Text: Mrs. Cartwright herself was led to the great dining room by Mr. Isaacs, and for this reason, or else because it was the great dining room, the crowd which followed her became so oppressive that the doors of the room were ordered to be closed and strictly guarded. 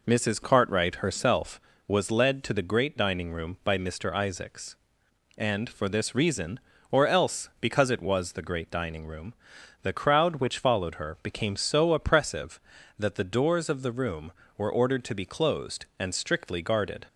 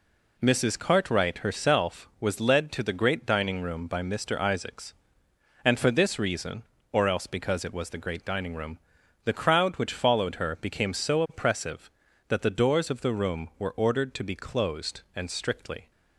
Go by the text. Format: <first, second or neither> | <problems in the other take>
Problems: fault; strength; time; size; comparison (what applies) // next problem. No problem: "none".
first | stops before "guarded"; at 15.9 s